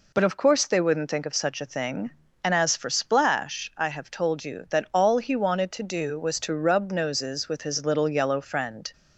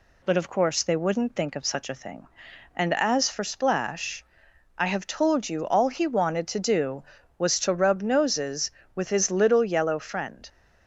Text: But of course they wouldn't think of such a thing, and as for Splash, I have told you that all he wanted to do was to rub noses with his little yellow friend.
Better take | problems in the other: first | skips "that"; at 5.6 s

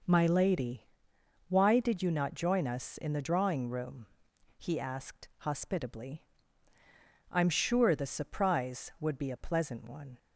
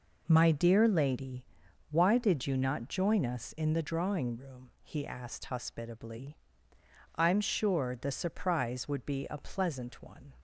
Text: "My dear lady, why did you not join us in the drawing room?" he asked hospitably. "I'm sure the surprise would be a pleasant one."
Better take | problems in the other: second | skips "dear"; at 0.2 s

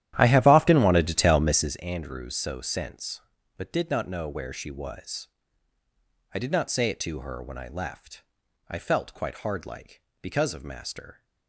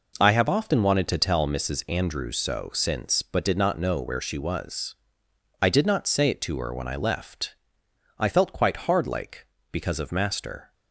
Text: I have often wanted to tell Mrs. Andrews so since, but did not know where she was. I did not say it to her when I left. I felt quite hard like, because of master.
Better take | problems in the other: second | starts louder than the rest; strong; until 1.8 s; 12 dB

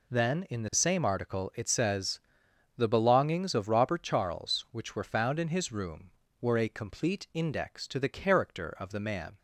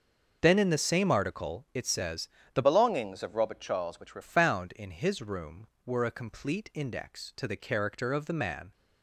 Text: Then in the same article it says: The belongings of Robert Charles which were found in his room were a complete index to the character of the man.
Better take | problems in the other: first | starts louder than the rest; until 1.4 s; 6 dB // changes voice from "belongings" to "were"; from 2.6 to 4.2 s; 1.6 s long

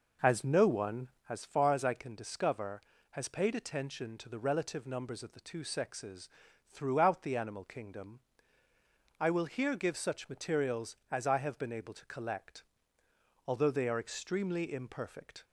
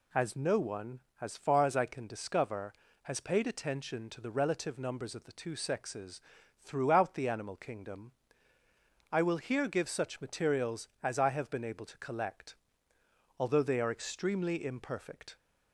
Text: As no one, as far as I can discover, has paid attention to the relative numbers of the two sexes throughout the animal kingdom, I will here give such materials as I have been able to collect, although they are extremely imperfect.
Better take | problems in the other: second | starts louder than the rest; noticeable; until 1.4 s; 5 dB // pauses between "sexes" and "throughout"; at 6.2 s; 0.38 s long; also in the second

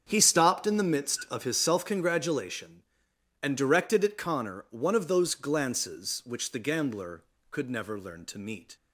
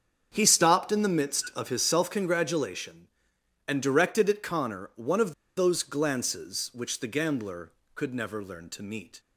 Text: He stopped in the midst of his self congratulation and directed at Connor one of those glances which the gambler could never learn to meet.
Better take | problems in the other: first | starts louder than the rest; strong; until 1.3 s; 7.5 dB; strong in the first // pauses between "of" and "those"; slight; at 5.3 s; 0.24 s long

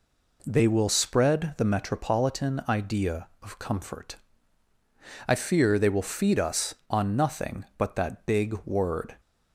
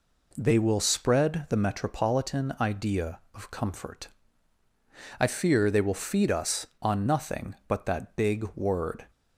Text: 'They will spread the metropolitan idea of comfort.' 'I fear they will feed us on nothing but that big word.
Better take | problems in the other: neither | none

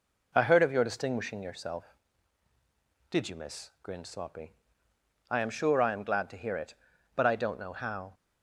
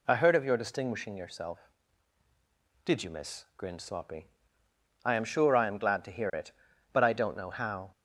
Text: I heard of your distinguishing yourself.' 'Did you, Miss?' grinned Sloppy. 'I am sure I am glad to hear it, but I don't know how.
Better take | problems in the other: second | starts louder than the rest; noticeable; until 2.0 s; 4 dB

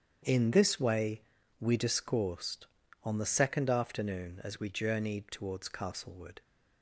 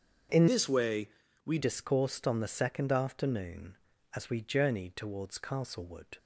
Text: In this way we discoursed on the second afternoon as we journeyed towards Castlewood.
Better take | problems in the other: first | starts louder than the rest; until 1.6 s; 7 dB; strong in the first // changes voice from "this" to "we"; from 0.4 to 1.5 s; 1.1 s long // pauses between "way" and "we"; slight; at 1.0 s; 0.36 s long; also in the first

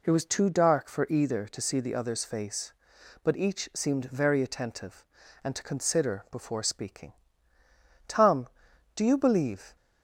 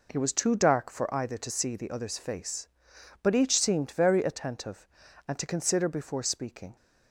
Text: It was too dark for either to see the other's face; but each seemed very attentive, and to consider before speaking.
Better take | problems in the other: second | goes on to say "Tom do you believe"; strong; from 8.0 s on; 1.6 s long

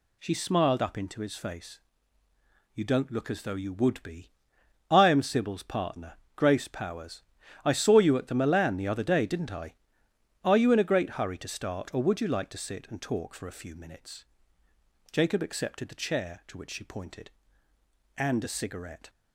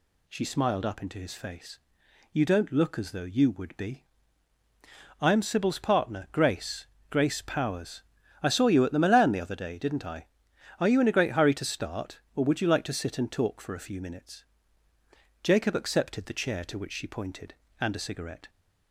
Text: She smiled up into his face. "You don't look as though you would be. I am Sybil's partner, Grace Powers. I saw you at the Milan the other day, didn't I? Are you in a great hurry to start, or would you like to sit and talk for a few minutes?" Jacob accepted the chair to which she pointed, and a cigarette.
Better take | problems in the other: first | says "Grace" twice; at 7.0 s

